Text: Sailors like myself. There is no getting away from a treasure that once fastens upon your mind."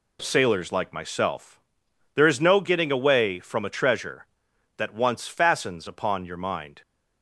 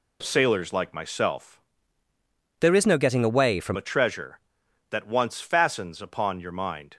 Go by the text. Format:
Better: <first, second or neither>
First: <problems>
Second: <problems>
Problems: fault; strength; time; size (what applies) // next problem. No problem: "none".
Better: first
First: none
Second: changes voice from "There" to "from"; from 2.5 to 3.7 s; 1.2 s long